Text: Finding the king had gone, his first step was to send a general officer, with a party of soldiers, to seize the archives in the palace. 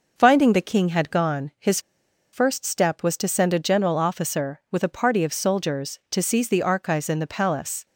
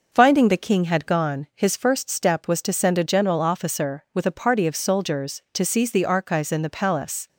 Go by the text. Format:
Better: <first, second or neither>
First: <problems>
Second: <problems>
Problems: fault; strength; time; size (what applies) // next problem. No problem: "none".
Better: second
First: pauses between "his" and "first"; noticeable; at 1.8 s; 0.51 s long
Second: none